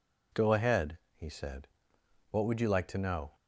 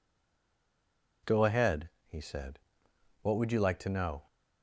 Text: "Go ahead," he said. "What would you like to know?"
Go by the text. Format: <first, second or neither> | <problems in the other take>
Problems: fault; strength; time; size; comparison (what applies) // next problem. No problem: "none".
first | stays silent before the first word; noticeable; until 1.2 s; 1.2 s long